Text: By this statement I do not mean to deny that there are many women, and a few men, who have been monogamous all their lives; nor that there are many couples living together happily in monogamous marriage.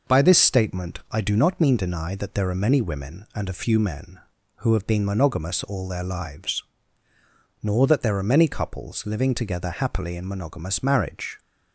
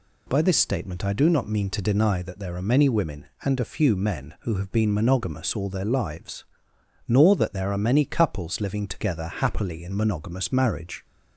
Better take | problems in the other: second | skips "to"; at 1.7 s

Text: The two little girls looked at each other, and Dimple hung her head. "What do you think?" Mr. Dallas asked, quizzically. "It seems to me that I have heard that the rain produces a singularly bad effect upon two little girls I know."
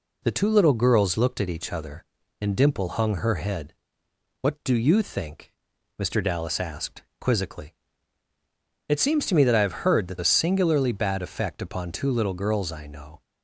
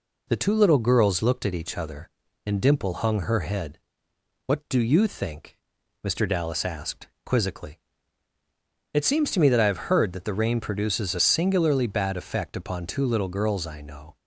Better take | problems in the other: second | skips "the rain produces"; at 10.1 s

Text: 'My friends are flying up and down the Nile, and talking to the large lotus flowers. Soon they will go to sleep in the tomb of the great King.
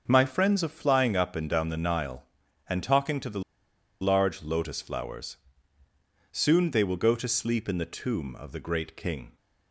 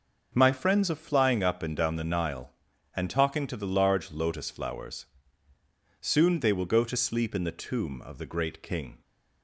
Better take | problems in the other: second | starts louder than the rest; until 1.0 s; 7 dB; also in the second // pauses between "the" and "large"; noticeable; at 3.4 s; 0.60 s long

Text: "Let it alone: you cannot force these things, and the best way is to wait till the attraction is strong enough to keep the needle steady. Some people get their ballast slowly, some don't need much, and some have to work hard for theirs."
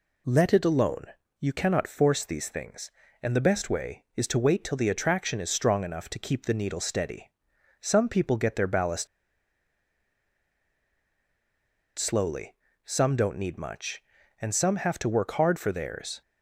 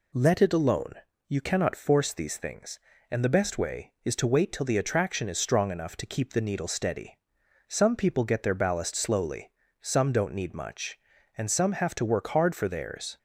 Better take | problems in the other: second | pauses between "ballast" and "slowly"; strong; at 9.0 s; 2.9 s long

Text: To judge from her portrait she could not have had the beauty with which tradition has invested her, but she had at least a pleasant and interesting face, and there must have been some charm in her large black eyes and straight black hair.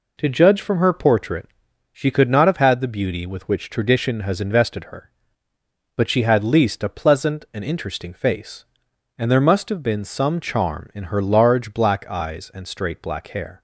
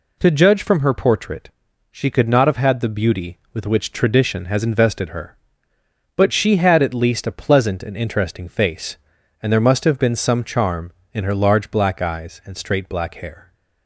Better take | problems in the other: second | pauses between "portrait" and "she"; noticeable; at 1.4 s; 0.46 s long; also in the second // skips "at"; at 6.4 s

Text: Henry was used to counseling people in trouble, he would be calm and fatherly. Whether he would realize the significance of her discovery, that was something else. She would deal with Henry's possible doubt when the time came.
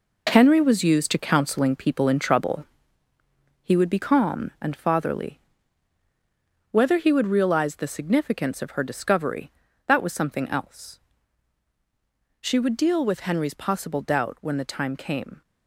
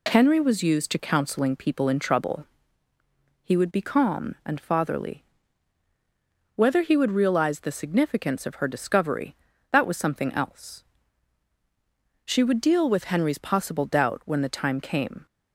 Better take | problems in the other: second | gets quieter; strong; throughout; 8.5 dB

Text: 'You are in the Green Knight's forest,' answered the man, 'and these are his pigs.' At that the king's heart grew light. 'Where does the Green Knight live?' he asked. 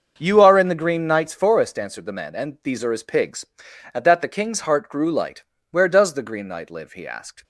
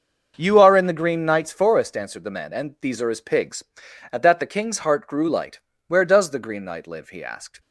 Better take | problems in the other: neither | starts louder than the rest; the same in both

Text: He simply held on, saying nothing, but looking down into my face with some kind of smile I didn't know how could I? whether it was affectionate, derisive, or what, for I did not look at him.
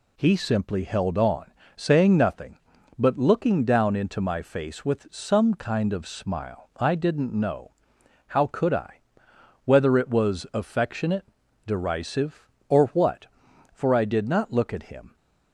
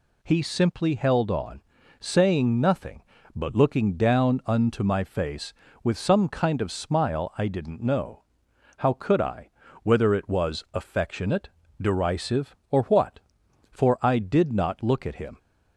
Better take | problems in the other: first | says "unto" for "into"; at 4.4 s // pauses between "know" and "how"; noticeable; at 8.2 s; 0.56 s long; noticeable in the first

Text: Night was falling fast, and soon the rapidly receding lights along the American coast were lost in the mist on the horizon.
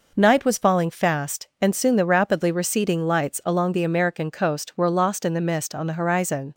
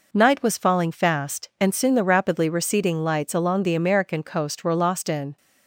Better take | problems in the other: first | stops before "the mist on the horizon"; at 5.3 s

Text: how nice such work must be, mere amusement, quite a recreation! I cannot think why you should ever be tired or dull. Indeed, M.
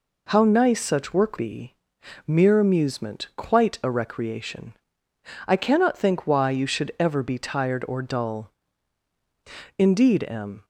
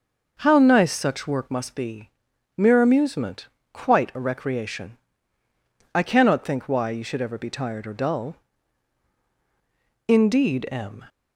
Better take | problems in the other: second | skips "must"; at 1.3 s

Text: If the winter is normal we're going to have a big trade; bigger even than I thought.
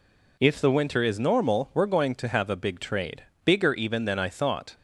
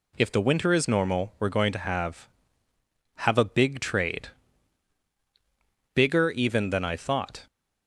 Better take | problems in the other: first | says "have" twice; at 3.1 s

